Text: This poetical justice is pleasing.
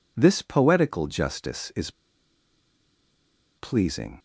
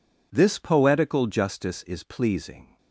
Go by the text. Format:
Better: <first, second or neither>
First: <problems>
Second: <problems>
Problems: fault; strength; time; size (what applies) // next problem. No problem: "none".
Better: second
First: pauses between "is" and "pleasing"; strong; at 1.9 s; 1.6 s long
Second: none